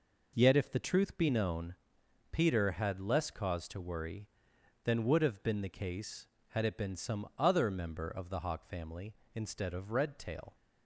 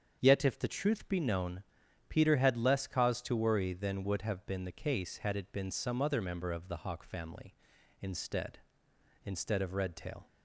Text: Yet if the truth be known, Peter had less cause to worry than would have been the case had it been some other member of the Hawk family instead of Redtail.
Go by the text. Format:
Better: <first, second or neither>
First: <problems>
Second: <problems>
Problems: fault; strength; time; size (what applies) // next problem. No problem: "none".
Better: first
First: none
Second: starts louder than the rest; strong; until 1.2 s; 7 dB // says "instead" twice; at 9.2 s